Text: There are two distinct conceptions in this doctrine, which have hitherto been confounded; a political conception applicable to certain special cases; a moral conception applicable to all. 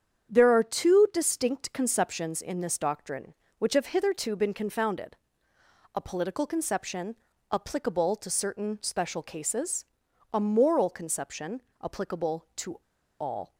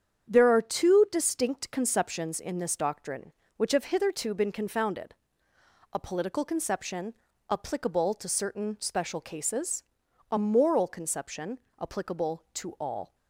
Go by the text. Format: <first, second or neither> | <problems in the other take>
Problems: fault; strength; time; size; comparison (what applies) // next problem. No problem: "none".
second | starts louder than the rest; strong; until 1.3 s; 8 dB; strong in the second // pauses between "conception" and "applicable"; slight; at 7.1 s; 0.34 s long; slight in the second // pauses between "conception" and "applicable"; slight; at 11.6 s; 0.20 s long; slight in the second // pauses between "to" and "all"; at 12.7 s; 0.42 s long